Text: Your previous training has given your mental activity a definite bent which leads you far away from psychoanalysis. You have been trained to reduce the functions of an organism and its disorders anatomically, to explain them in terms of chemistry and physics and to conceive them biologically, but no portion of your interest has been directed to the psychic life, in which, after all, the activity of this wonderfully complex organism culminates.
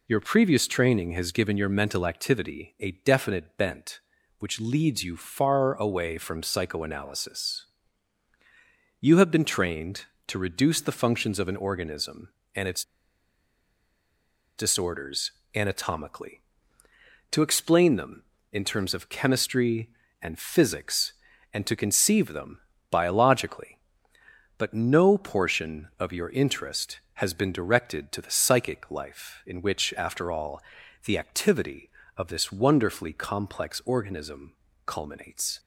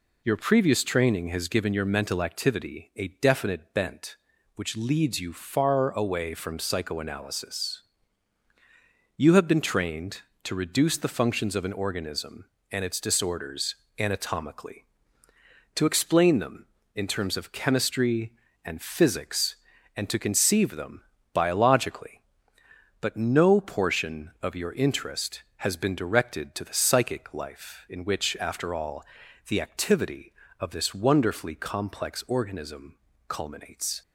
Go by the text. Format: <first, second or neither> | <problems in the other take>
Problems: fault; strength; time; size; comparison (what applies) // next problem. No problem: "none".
second | pauses between "its" and "disorders"; strong; at 12.8 s; 1.7 s long // pauses between "disorders" and "anatomically"; slight; at 15.3 s; 0.24 s long; slight in the second // pauses between "them" and "biologically"; slight; at 22.5 s; 0.30 s long; slight in the second // pauses between "organism" and "culminates"; slight; at 34.5 s; 0.32 s long; slight in the second